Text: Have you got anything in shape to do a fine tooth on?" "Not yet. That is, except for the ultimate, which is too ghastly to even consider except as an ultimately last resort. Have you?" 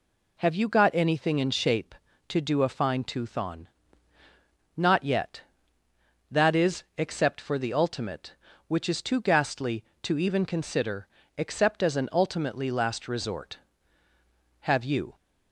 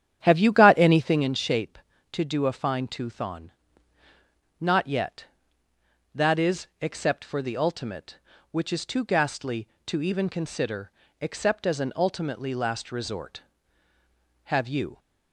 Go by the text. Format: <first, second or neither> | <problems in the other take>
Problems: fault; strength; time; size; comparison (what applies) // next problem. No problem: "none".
first | starts louder than the rest; strong; until 1.3 s; 9.5 dB // pauses between "consider" and "except"; slight; at 10.9 s; 0.32 s long; slight in the first